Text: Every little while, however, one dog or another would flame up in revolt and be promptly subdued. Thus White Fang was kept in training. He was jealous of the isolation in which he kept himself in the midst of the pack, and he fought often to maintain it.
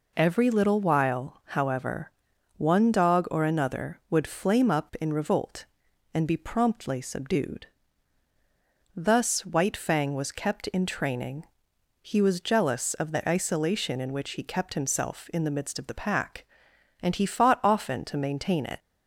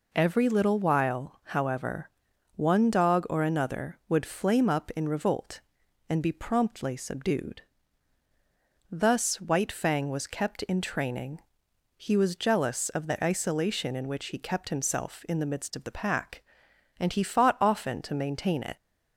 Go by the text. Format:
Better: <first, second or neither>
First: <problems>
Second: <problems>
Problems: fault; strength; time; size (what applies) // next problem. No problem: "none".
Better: neither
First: none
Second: none